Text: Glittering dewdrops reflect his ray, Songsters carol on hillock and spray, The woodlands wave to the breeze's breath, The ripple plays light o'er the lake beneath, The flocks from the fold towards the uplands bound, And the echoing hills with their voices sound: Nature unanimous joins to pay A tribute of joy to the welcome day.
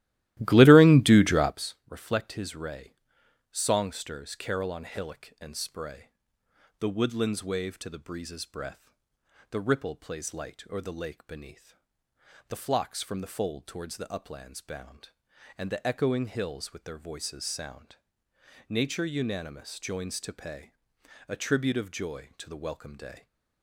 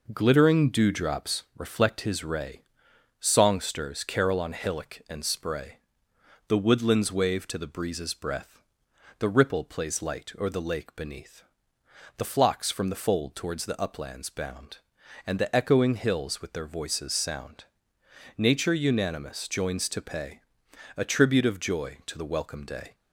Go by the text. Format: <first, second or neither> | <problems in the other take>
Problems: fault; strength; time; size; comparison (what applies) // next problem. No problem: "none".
second | starts louder than the rest; strong; until 1.6 s; 16 dB // pauses between "pay" and "A"; noticeable; at 20.6 s; 0.58 s long; noticeable in the second